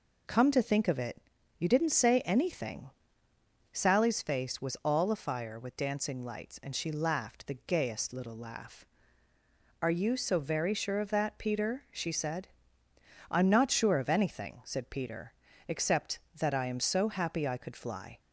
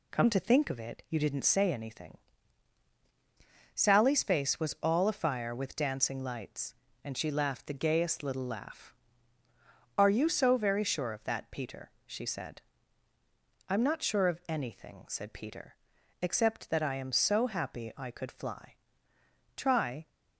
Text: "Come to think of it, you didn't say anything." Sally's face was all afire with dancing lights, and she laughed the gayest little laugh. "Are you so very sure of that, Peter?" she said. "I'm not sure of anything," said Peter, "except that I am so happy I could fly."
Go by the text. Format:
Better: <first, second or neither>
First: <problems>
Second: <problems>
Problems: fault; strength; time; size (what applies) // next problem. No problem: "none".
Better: first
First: none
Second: goes on to say "Try"; from 19.5 s on; 0.52 s long